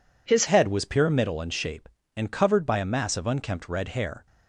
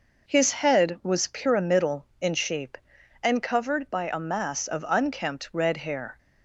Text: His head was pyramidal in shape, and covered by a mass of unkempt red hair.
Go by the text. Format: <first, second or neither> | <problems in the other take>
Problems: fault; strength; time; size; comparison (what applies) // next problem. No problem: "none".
second | changes voice at "head"; from 0.4 s on; 3.8 s long